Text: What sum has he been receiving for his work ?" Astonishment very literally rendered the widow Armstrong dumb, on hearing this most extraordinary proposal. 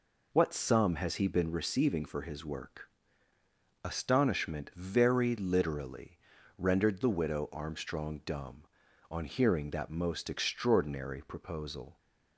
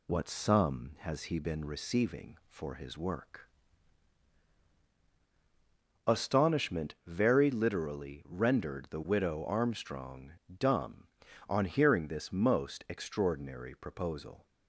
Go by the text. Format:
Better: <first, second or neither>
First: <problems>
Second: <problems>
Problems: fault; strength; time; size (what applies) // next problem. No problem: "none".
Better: second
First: pauses between "literally" and "rendered"; at 6.1 s; 0.38 s long // says "that" for "this"; at 9.7 s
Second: none